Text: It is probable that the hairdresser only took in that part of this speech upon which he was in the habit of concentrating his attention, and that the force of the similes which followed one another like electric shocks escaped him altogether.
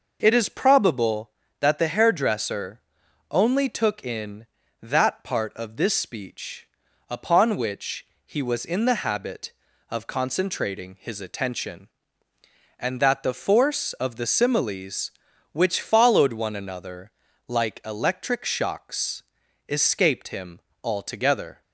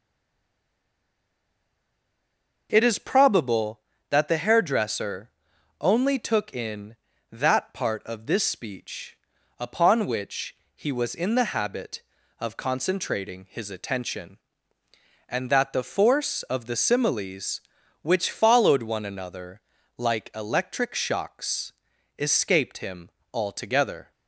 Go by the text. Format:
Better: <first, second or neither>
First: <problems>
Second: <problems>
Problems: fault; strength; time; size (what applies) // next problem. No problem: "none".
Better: first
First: pauses between "hairdresser" and "only"; noticeable; at 2.8 s; 0.50 s long // pauses between "speech" and "upon"; at 6.6 s; 0.42 s long // pauses between "which" and "he"; slight; at 8.0 s; 0.22 s long // pauses between "another" and "like"; at 17.0 s; 0.38 s long // pauses between "shocks" and "escaped"; noticeable; at 19.2 s; 0.46 s long // pauses between "him" and "altogether"; slight; at 20.5 s; 0.24 s long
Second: stays silent before the first word; strong; until 2.6 s; 2.6 s long // pauses between "hairdresser" and "only"; noticeable; at 5.3 s; 0.50 s long // pauses between "speech" and "upon"; at 9.1 s; 0.42 s long // pauses between "which" and "he"; slight; at 10.5 s; 0.22 s long // pauses between "another" and "like"; at 19.5 s; 0.38 s long // pauses between "shocks" and "escaped"; noticeable; at 21.7 s; 0.46 s long // pauses between "him" and "altogether"; slight; at 23.0 s; 0.24 s long